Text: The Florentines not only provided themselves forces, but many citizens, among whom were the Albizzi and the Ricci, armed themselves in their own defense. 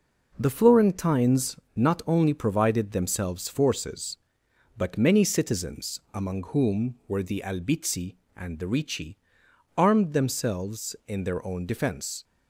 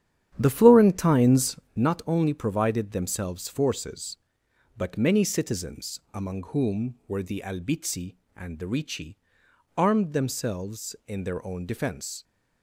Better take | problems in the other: first | starts louder than the rest; strong; until 1.9 s; 10 dB // pauses between "Florentines" and "not"; slight; at 1.5 s; 0.18 s long; slight in the first

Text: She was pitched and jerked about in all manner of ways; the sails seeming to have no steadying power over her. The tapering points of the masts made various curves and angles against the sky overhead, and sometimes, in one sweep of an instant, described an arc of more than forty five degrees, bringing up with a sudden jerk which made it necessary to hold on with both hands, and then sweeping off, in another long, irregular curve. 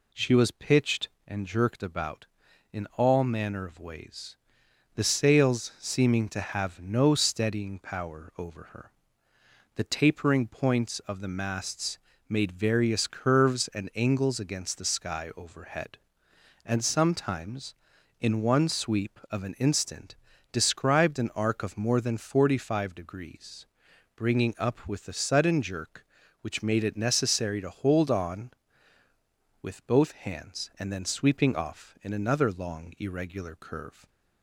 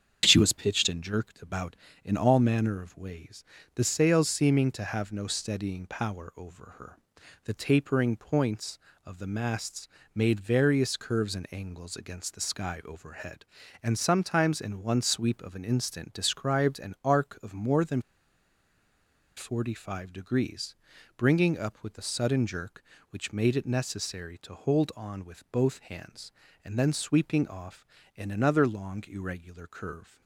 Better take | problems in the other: first | starts louder than the rest; strong; until 1.2 s; 8 dB // pauses between "masts" and "made"; slight; at 9.8 s; 0.28 s long; slight in the first // pauses between "than" and "forty"; strong; at 18.0 s; 1.3 s long

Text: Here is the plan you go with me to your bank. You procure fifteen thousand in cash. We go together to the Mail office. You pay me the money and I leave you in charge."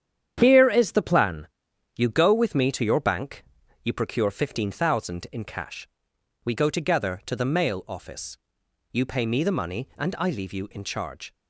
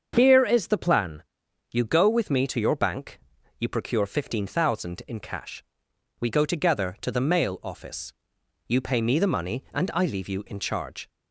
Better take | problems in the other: second | gets quieter; throughout; 7 dB // starts louder than the rest; strong; until 1.4 s; 9 dB; also in the second // pauses between "plan" and "you"; noticeable; at 1.4 s; 0.48 s long; noticeable in the second

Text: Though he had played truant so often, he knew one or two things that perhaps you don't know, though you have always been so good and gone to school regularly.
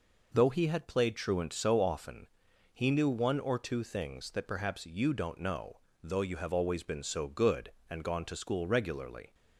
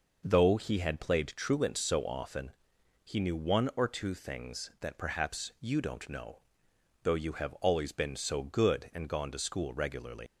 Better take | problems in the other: first | leaves "regularly" unfinished; at 10.2 s; 120 ms

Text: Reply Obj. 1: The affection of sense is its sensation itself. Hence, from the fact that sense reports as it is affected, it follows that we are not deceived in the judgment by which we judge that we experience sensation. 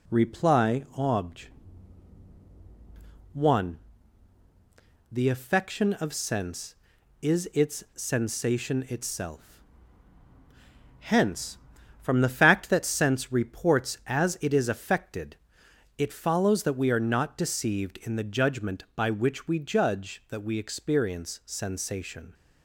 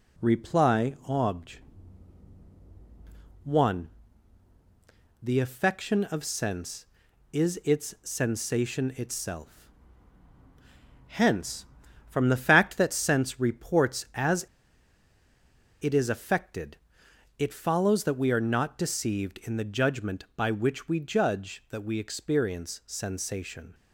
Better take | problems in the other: first | pauses between "as" and "it"; strong; at 14.4 s; 1.3 s long

